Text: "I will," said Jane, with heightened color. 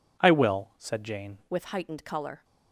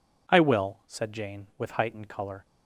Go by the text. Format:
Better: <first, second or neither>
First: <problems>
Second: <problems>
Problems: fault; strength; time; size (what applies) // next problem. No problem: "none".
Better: second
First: changes voice at "with"; from 1.5 s on; 0.9 s long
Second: none